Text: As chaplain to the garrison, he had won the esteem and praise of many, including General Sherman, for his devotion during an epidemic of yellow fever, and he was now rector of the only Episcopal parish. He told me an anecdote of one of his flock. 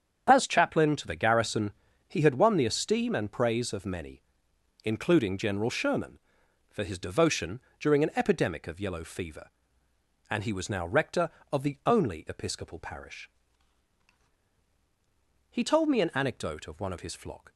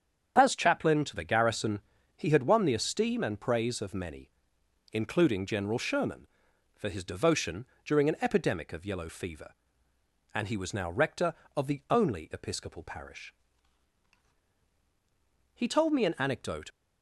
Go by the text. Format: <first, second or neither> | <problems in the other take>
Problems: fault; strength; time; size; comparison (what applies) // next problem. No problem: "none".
first | starts louder than the rest; strong; until 1.3 s; 8 dB; strong in the first // pauses between "devotion" and "during"; slight; at 7.6 s; 0.22 s long; slight in the first // stops before "of one of his flock"; at 16.6 s